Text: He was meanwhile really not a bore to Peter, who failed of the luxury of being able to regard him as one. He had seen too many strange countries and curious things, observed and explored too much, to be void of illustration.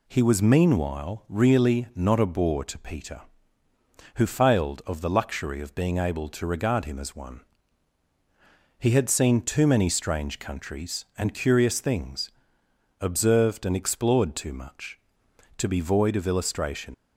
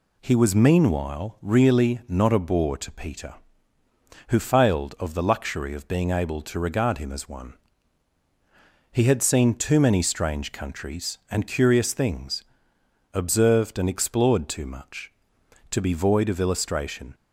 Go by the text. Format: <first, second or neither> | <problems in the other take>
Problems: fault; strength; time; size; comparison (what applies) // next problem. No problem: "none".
second | leaves "illustration" unfinished; at 16.9 s; 65 ms